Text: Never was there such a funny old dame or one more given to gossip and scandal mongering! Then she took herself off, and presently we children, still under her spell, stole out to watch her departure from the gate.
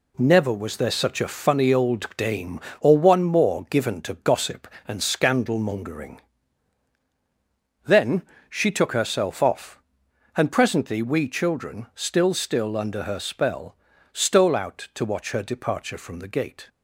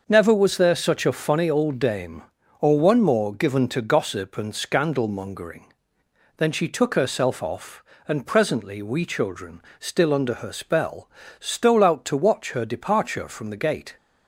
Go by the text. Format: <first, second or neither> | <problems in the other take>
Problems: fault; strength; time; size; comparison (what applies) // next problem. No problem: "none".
second | pauses between "Then" and "she"; slight; at 8.2 s; 0.26 s long // says "still" twice; at 12.3 s